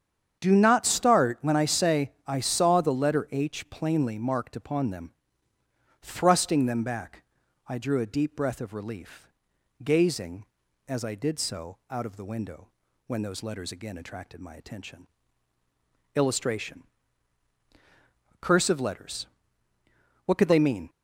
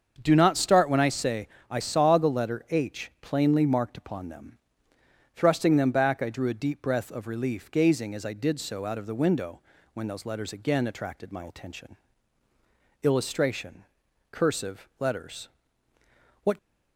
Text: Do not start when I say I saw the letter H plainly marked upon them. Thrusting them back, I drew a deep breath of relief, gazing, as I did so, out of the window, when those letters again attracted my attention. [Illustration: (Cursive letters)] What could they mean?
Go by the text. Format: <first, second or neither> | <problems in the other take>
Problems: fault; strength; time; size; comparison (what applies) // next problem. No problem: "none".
first | starts louder than the rest; until 1.2 s; 7 dB; strong in the first // pauses between "say" and "I"; slight; at 1.4 s; 0.22 s long // stops before "could they mean"; at 16.5 s